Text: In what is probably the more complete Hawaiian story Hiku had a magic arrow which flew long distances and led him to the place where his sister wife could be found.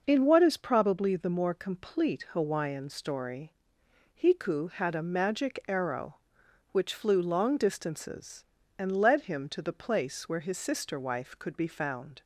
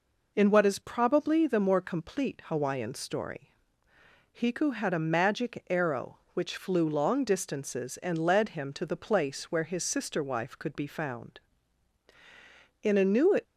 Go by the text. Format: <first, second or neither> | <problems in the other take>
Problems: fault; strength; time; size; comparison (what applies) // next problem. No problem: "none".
first | pauses between "story" and "Hiku"; noticeable; at 3.5 s; 0.80 s long; noticeable in the first // goes on to say "In a New"; from 12.8 s on; 0.56 s long